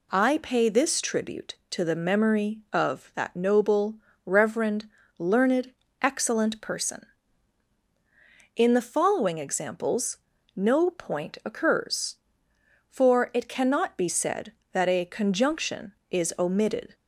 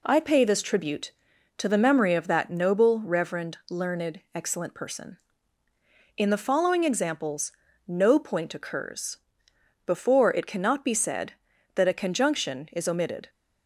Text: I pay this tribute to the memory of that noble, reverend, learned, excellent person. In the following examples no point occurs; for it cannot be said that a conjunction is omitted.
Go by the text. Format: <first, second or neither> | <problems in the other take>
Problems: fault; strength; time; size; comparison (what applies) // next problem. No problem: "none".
first | pauses between "examples" and "no"; slight; at 7.5 s; 0.34 s long; also in the first // says "before" for "for"; at 9.8 s